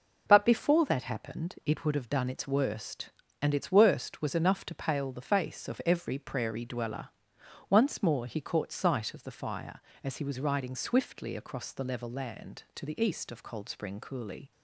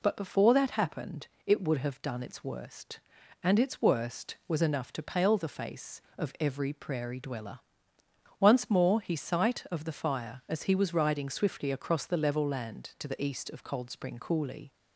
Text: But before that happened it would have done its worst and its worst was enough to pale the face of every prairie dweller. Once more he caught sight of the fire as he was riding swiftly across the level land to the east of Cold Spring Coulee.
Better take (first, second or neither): first